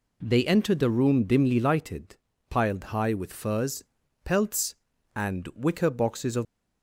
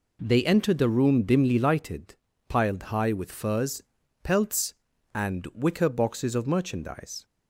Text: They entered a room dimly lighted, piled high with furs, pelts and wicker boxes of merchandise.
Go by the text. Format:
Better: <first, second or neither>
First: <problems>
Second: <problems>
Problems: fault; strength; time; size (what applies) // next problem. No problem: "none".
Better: second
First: stops before "merchandise"; at 6.4 s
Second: none